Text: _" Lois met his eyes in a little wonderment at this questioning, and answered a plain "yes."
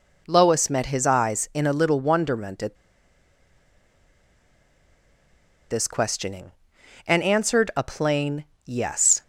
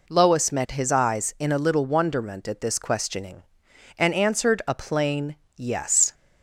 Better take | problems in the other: second | pauses between "at" and "this"; strong; at 2.7 s; 2.9 s long // pauses between "plain" and "yes"; slight; at 8.4 s; 0.20 s long; slight in the second

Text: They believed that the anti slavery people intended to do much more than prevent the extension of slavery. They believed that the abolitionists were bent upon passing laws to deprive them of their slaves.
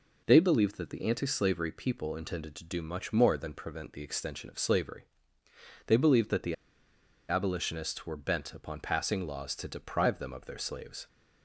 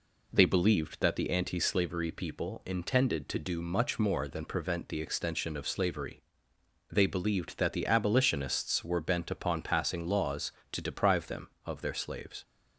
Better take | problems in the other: second | pauses between "the" and "abolitionists"; noticeable; at 6.5 s; 0.74 s long

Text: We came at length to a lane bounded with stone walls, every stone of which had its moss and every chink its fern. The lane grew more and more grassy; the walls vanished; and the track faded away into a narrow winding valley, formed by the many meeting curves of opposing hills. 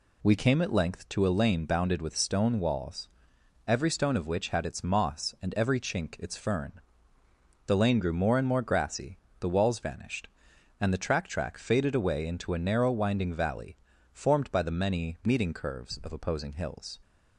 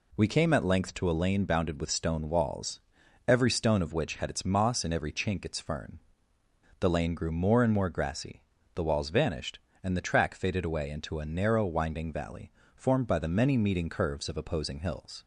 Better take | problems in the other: second | says "track" twice; at 11.2 s

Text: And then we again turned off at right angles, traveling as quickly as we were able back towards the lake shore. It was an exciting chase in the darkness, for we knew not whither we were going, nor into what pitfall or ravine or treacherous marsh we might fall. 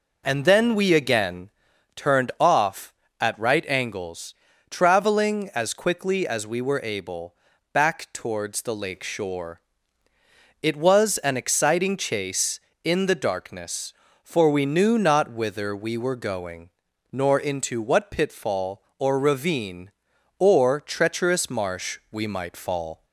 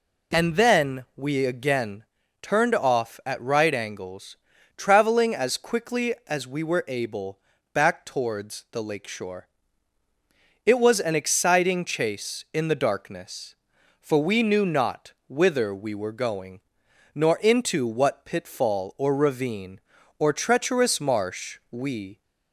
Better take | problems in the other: first | pauses between "again" and "turned"; slight; at 2.0 s; 0.36 s long; also in the first // pauses between "able" and "back"; slight; at 7.3 s; 0.36 s long; also in the first // pauses between "not" and "whither"; slight; at 15.1 s; 0.16 s long // stops before "might fall"; at 22.2 s

